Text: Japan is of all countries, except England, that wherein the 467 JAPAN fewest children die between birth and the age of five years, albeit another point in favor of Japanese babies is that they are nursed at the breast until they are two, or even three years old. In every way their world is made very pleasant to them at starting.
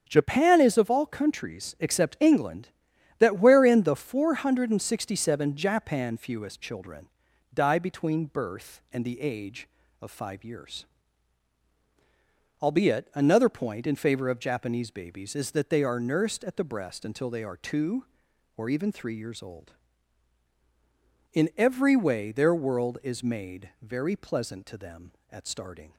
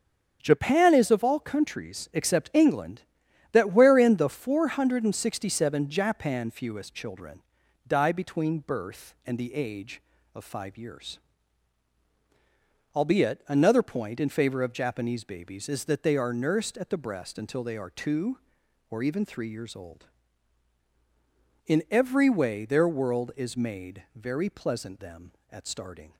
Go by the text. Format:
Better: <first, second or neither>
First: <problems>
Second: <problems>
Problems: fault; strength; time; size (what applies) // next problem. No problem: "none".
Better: first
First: starts louder than the rest; strong; until 1.0 s; 7.5 dB // pauses between "children" and "die"; noticeable; at 7.0 s; 0.46 s long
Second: starts louder than the rest; strong; until 1.4 s; 7.5 dB // pauses between "children" and "die"; noticeable; at 7.4 s; 0.46 s long // skips "to"; at 24.9 s